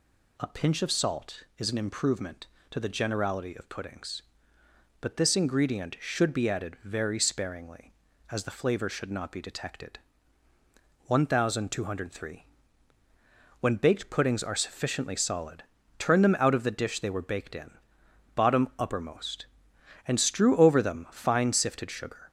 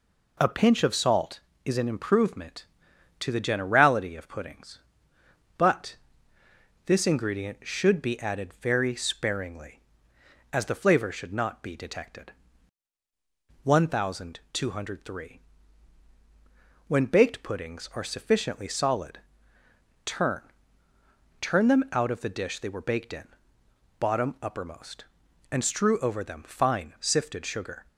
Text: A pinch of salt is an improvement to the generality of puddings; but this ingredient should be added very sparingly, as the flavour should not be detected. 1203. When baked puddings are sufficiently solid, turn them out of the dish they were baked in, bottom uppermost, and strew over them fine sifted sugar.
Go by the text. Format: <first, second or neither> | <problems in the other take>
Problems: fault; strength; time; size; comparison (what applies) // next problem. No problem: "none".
first | pauses between "but" and "this"; noticeable; at 5.9 s; 0.88 s long // says "turn" twice; at 21.4 s